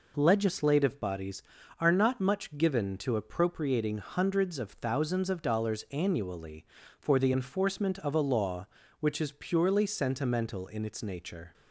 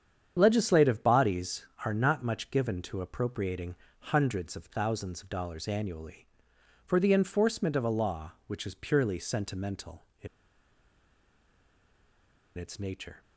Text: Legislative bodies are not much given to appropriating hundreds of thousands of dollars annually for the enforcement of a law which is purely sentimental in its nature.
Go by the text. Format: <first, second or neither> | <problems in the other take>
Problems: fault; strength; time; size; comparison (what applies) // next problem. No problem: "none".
first | starts louder than the rest; strong; until 1.3 s; 8.5 dB // pauses between "appropriating" and "hundreds"; at 3.7 s; 0.40 s long // pauses between "in" and "its"; strong; at 10.2 s; 2.3 s long